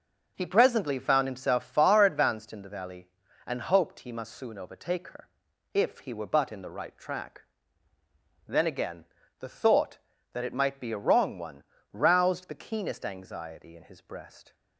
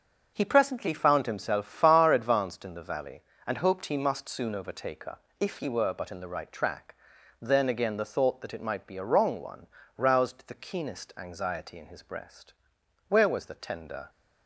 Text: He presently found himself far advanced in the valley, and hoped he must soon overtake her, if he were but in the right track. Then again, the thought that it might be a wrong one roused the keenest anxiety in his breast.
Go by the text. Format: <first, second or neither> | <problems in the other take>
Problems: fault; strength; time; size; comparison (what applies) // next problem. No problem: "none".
first | starts louder than the rest; noticeable; until 1.3 s; 6 dB; also in the first // pauses between "one" and "roused"; slight; at 9.6 s; 0.28 s long; slight in the first // goes on to say "Where was the tender"; noticeable; from 13.0 s on; 1.0 s long